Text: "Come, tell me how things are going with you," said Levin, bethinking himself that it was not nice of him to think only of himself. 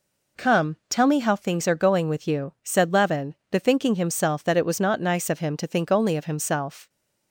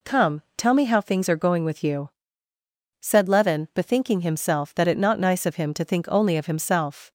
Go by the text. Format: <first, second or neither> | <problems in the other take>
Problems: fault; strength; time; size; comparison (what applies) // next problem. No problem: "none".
first | skips "was"; at 4.9 s